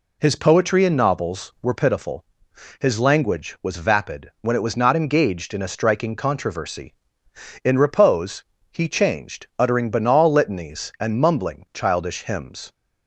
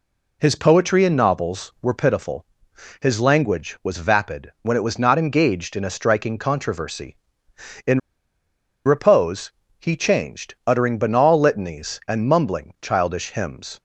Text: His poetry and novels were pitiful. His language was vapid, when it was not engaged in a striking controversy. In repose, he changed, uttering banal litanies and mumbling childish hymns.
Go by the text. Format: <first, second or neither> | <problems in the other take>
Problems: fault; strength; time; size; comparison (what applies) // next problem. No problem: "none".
first | pauses between "In" and "repose"; noticeable; at 7.9 s; 0.86 s long